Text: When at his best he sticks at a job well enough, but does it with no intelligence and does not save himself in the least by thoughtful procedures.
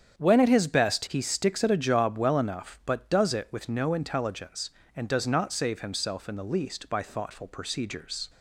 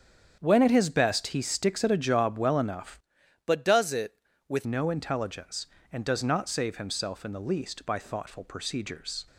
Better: first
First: starts louder than the rest; strong; until 1.2 s; 8 dB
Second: starts louder than the rest; strong; until 1.4 s; 8 dB // changes voice from "but" to "with"; from 3.4 to 4.6 s; 1.2 s long

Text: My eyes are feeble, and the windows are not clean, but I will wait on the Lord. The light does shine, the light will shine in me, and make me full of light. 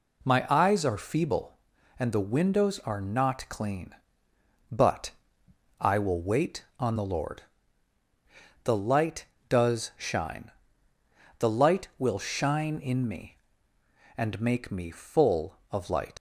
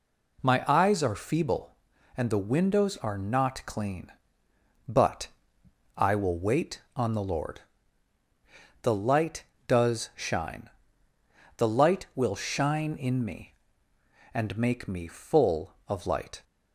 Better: second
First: pauses between "but" and "I"; noticeable; at 5.0 s; 0.70 s long // leaves "light" unfinished; at 16.1 s; 90 ms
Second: pauses between "but" and "I"; noticeable; at 5.2 s; 0.70 s long

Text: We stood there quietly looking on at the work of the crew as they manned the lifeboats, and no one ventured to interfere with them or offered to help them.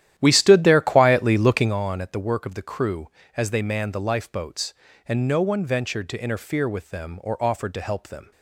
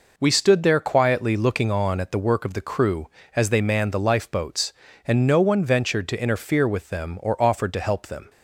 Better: second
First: starts louder than the rest; strong; until 1.8 s; 12 dB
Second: none

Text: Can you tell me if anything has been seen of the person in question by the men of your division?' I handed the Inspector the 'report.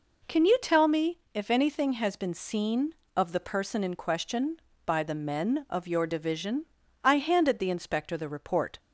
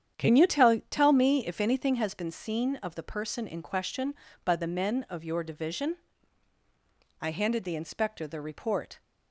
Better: first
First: none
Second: starts louder than the rest; strong; until 1.2 s; 9 dB // says "tell" twice; at 0.9 s

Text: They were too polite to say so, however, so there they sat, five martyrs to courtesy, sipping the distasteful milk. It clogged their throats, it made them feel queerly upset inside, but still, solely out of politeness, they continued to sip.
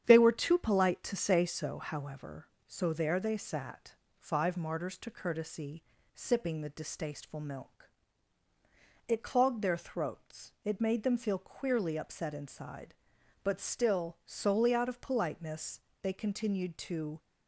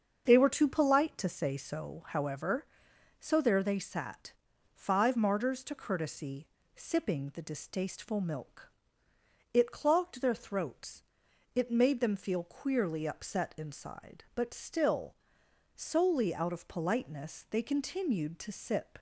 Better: second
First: starts louder than the rest; strong; until 1.0 s; 9 dB // stops before "sip"; at 17.1 s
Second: starts louder than the rest; until 1.2 s; 7 dB

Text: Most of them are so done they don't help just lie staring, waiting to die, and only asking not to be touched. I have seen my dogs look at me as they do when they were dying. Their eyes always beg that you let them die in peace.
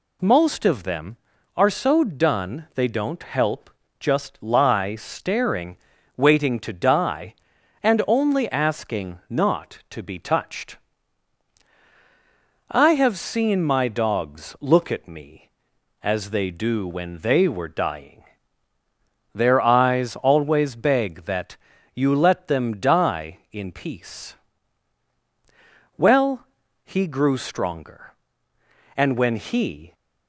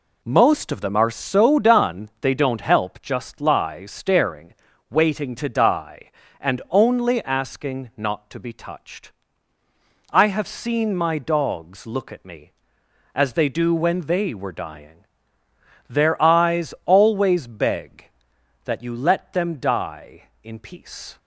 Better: second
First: pauses between "help" and "just"; slight; at 3.6 s; 0.30 s long // pauses between "that" and "you"; at 21.5 s; 0.40 s long // goes on to say "Well he grew stronger and when he"; strong; from 25.9 s on; 3.9 s long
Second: none

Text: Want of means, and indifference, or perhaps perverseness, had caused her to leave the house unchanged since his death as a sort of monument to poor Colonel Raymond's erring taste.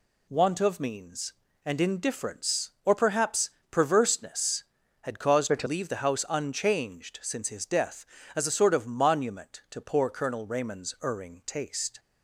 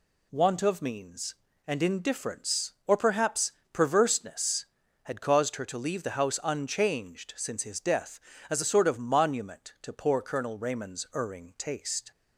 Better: second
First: pauses between "perhaps" and "perverseness"; slight; at 3.4 s; 0.22 s long // changes voice from "her" to "to"; from 5.4 to 5.6 s; 0.2 s long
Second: pauses between "perhaps" and "perverseness"; slight; at 3.5 s; 0.22 s long

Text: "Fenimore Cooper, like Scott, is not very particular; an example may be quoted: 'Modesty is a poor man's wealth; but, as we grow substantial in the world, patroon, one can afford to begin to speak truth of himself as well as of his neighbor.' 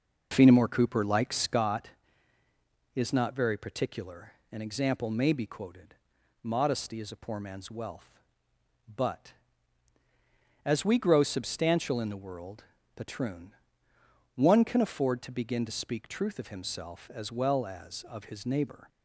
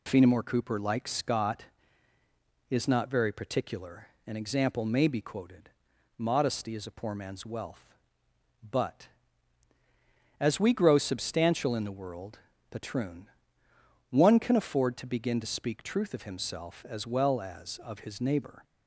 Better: second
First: starts louder than the rest; noticeable; until 1.7 s; 5 dB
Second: none

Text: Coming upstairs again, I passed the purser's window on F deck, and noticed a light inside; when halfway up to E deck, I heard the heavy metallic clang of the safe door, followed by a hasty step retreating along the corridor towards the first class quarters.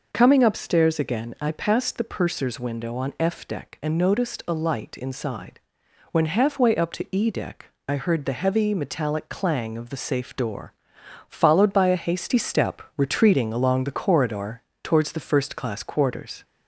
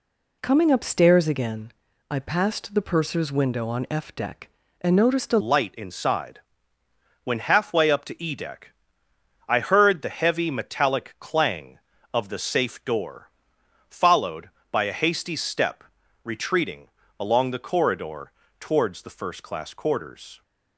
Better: first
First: pauses between "corridor" and "towards"; slight; at 14.6 s; 0.22 s long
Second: changes voice at "light"; from 5.4 s on; 15.0 s long // pauses between "step" and "retreating"; at 15.8 s; 0.42 s long // pauses between "retreating" and "along"; slight; at 16.8 s; 0.30 s long // pauses between "corridor" and "towards"; slight; at 18.2 s; 0.30 s long

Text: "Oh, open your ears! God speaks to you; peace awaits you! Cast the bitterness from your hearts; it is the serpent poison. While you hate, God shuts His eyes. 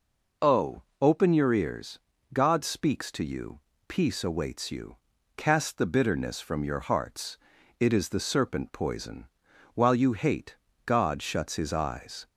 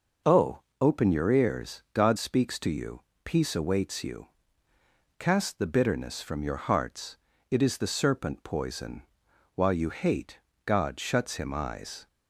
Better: first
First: none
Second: says "Him" for "His"; at 11.3 s

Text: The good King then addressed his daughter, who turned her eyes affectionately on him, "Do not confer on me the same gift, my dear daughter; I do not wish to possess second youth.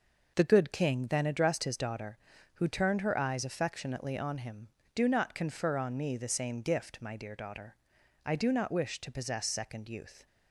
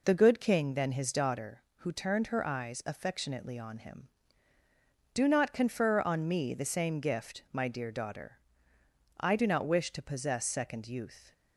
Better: first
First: none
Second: skips "addressed"; at 0.9 s

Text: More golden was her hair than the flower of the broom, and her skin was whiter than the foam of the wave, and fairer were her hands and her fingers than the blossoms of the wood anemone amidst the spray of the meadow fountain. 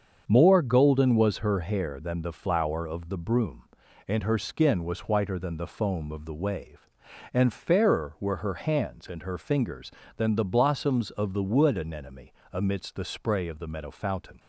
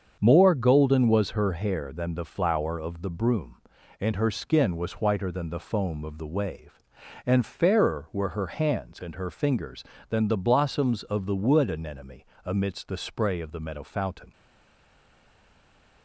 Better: first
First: starts louder than the rest; until 1.2 s; 7 dB // pauses between "anemone" and "amidst"; slight; at 12.3 s; 0.20 s long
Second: starts louder than the rest; until 1.2 s; 7 dB // pauses between "anemone" and "amidst"; slight; at 12.2 s; 0.20 s long // stays silent after the last word; noticeable; from 14.3 s on; 1.7 s long

